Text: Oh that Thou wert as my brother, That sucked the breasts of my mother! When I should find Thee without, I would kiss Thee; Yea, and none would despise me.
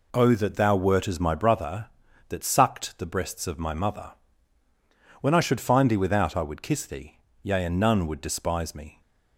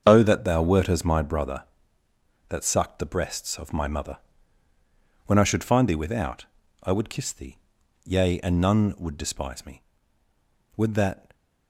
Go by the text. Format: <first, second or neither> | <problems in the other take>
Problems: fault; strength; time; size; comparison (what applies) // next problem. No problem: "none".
first | starts louder than the rest; strong; until 1.0 s; 7 dB // goes on to say "Would that"; from 10.7 s on; 0.58 s long